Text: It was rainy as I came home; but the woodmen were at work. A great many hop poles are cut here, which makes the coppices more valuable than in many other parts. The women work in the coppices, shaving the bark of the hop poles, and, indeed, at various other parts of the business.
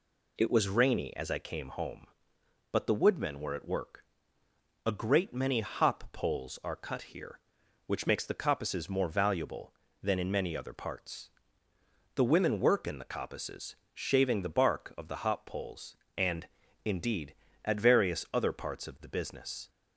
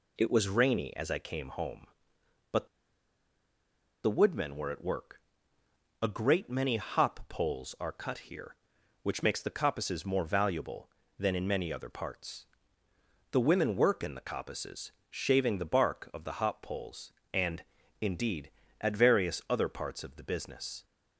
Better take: first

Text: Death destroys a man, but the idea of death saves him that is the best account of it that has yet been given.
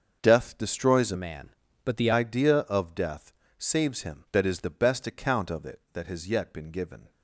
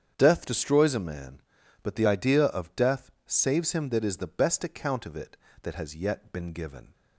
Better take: second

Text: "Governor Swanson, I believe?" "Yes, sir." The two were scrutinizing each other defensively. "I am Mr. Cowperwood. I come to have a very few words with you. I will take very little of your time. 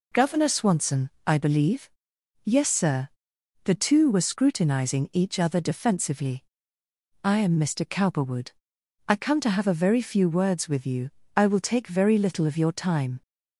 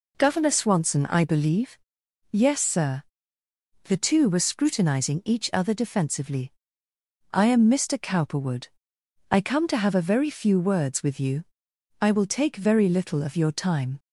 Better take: neither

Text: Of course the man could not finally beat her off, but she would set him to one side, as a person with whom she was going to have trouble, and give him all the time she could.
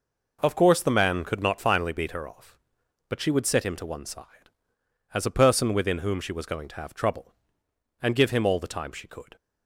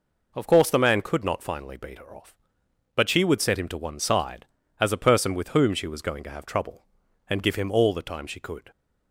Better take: second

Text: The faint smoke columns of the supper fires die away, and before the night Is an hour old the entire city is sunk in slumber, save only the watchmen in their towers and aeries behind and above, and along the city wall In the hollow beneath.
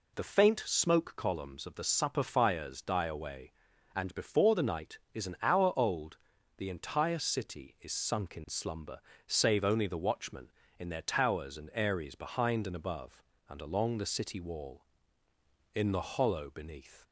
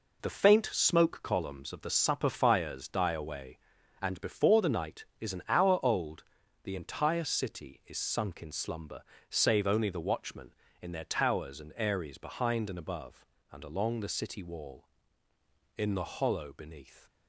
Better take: first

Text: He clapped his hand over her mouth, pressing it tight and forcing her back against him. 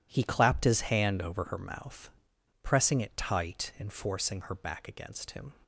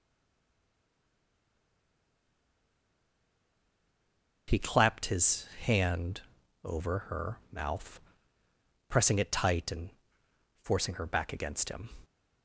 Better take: first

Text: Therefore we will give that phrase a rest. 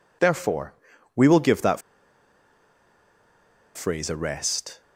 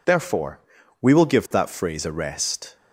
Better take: second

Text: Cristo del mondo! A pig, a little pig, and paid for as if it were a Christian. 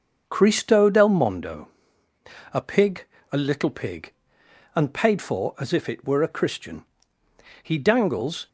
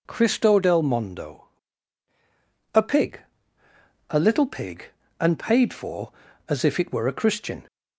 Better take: second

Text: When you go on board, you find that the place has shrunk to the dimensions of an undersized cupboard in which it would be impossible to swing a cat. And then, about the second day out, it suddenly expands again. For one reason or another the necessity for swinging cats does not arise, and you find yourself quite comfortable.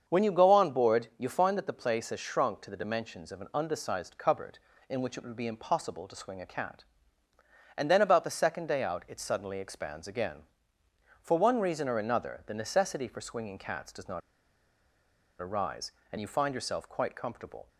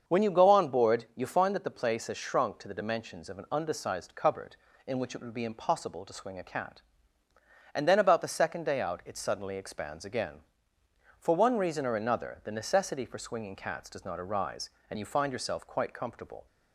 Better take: second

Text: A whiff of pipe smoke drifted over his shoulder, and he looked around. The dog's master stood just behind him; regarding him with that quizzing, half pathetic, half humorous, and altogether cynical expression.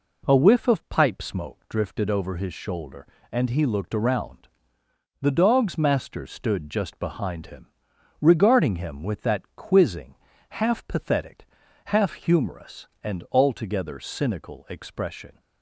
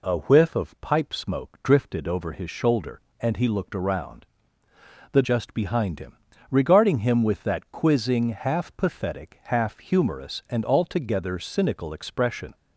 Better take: first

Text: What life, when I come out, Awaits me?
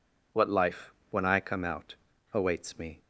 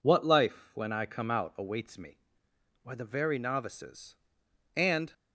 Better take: first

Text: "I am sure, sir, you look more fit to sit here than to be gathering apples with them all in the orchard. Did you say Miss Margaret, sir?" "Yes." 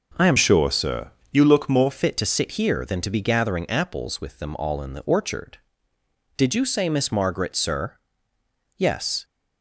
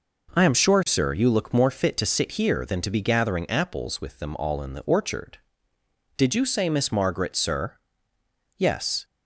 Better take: second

